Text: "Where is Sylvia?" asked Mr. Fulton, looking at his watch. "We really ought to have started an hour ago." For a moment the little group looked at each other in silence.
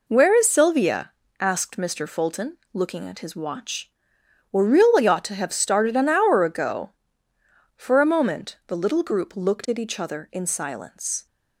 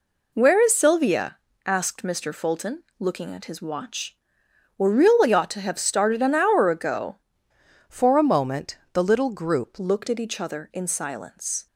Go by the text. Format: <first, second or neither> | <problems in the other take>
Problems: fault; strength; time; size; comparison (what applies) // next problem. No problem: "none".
first | changes voice from "For" to "group"; from 7.8 to 9.7 s; 1.9 s long // pauses between "moment" and "the"; slight; at 8.7 s; 0.18 s long